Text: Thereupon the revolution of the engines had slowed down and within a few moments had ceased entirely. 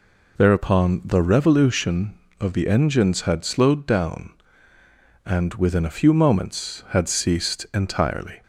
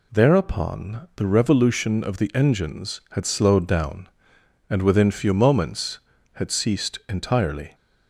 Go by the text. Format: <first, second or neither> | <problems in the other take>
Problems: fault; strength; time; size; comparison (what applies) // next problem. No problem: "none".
first | skips "a"; at 5.1 s